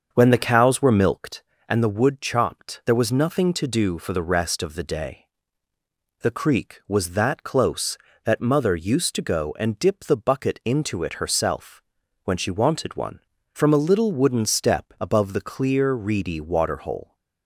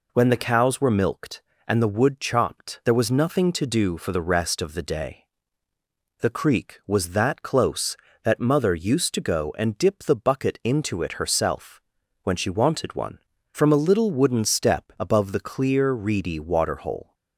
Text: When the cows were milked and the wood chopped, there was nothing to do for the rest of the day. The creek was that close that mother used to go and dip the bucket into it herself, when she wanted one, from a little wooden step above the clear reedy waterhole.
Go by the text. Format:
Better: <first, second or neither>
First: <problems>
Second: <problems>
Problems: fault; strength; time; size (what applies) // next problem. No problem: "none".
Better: second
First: starts louder than the rest; until 1.4 s; 6.5 dB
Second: none